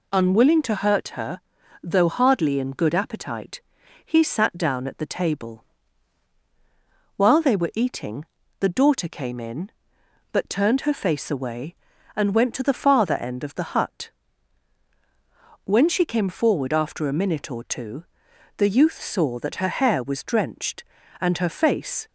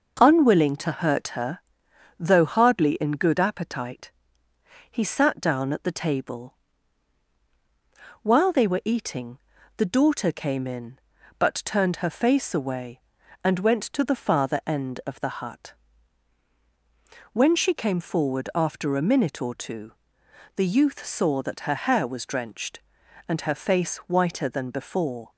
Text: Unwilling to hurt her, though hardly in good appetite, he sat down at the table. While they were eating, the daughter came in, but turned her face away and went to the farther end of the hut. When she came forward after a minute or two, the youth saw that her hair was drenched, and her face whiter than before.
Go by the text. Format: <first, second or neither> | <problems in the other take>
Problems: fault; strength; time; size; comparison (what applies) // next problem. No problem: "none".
second | stops before "whiter than before"; at 22.0 s